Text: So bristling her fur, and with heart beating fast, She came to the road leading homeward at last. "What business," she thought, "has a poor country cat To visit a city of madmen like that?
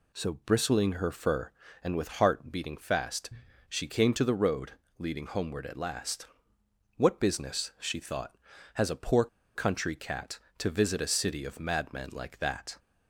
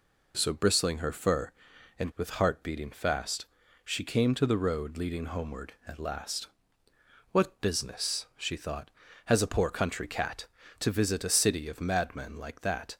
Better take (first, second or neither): second